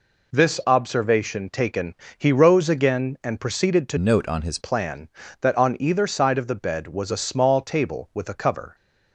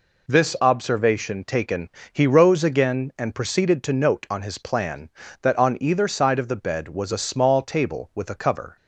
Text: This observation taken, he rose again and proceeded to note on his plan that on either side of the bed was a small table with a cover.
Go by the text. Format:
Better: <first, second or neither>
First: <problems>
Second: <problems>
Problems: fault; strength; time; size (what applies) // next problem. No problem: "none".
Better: second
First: changes voice from "note" to "his"; from 3.9 to 4.5 s; 0.6 s long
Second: none